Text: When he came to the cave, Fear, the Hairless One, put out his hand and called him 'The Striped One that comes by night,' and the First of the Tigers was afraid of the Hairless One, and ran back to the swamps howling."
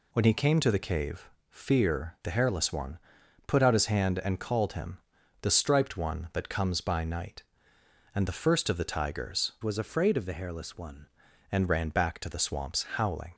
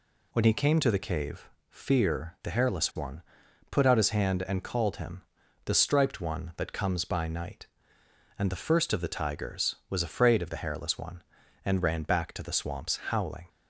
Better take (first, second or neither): second